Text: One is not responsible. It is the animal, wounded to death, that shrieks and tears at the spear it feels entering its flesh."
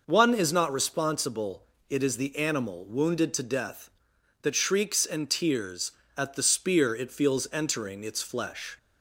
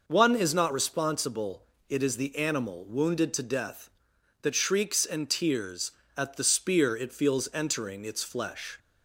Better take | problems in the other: neither | none

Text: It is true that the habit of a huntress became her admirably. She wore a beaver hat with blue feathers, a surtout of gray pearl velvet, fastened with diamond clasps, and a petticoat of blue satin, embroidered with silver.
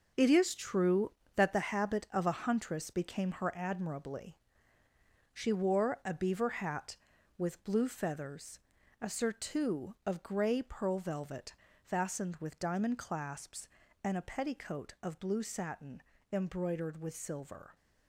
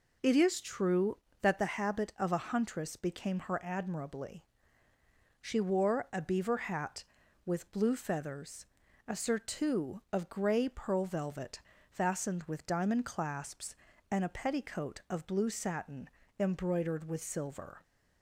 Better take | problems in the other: second | gets quieter; strong; throughout; 9 dB

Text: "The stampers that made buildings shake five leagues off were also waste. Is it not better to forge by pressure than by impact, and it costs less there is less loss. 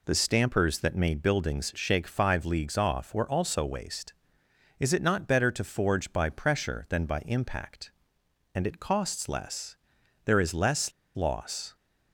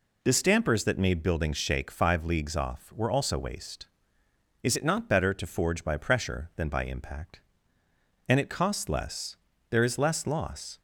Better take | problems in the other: second | pauses between "less" and "there"; noticeable; at 9.7 s; 0.50 s long; slight in the second // pauses between "less" and "loss"; slight; at 10.9 s; 0.24 s long

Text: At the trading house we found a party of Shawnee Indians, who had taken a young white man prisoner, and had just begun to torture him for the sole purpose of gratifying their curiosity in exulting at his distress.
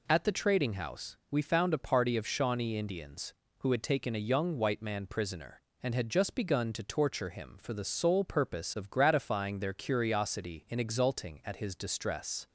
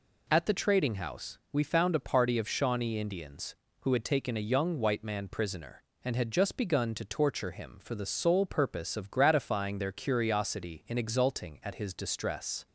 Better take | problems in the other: neither | pauses between "house" and "we"; slight; the same in both

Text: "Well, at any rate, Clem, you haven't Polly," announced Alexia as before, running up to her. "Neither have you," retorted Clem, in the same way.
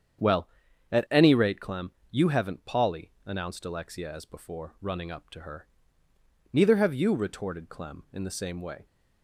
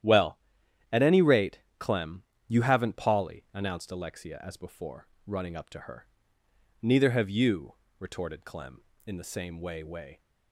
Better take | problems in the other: first | starts louder than the rest; strong; until 1.5 s; 11 dB; strong in the first // says "way" twice; at 9.8 s

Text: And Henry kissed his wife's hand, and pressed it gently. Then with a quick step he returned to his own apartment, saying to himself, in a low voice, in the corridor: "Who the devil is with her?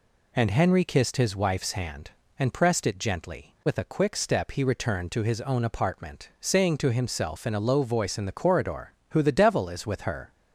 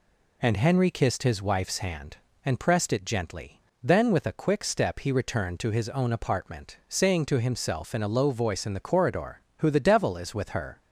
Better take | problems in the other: second | skips "Then"; at 3.5 s

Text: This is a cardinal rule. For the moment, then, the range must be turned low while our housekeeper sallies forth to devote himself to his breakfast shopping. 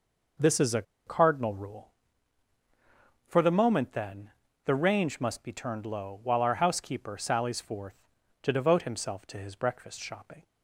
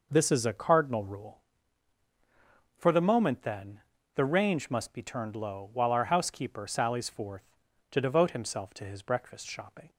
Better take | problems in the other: second | pauses between "a" and "cardinal"; slight; at 0.8 s; 0.23 s long

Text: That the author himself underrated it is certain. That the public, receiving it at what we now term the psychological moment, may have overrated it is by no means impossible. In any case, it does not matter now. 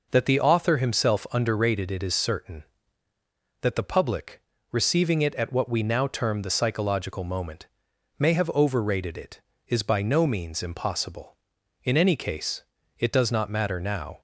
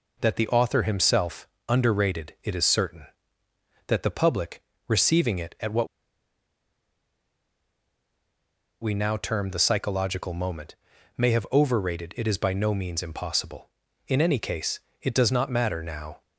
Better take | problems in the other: first | pauses between "himself" and "underrated"; slight; at 1.4 s; 0.20 s long // pauses between "what" and "we"; strong; at 5.8 s; 2.9 s long

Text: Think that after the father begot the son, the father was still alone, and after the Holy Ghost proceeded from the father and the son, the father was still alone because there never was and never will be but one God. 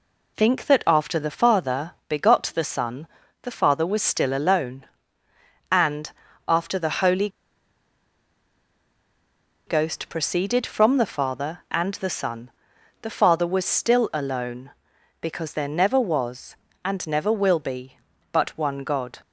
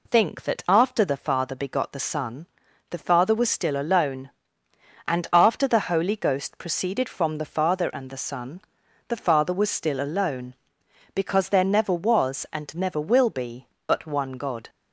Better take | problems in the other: second | pauses between "father" and "begot"; slight; at 1.9 s; 0.16 s long // pauses between "and" and "after"; at 6.0 s; 0.38 s long // pauses between "Holy" and "Ghost"; strong; at 7.2 s; 2.3 s long

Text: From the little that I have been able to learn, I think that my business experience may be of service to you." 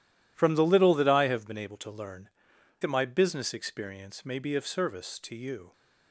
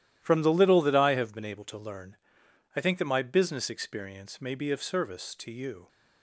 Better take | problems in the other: second | skips "I think"; at 2.5 s

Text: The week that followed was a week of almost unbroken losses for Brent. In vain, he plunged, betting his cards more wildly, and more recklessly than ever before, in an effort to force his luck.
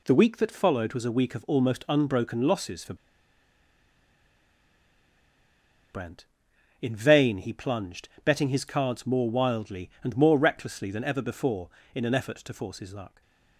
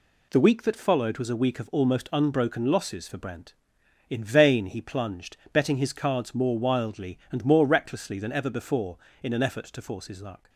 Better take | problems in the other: second | pauses between "for" and "Brent"; strong; at 2.9 s; 2.9 s long // stays silent after the last word; slight; from 13.0 s on; 0.5 s long

